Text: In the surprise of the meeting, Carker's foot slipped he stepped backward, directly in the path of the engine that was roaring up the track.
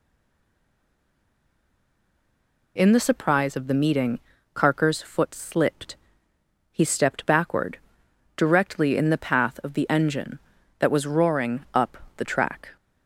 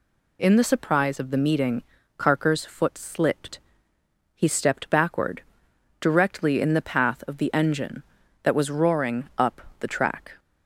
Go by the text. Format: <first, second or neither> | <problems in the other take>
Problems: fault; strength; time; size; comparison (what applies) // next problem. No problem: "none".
second | stays silent before the first word; strong; until 2.7 s; 2.7 s long // pauses between "slipped" and "he"; noticeable; at 5.9 s; 0.74 s long; noticeable in the second // pauses between "up" and "the"; slight; at 11.9 s; 0.22 s long; slight in the second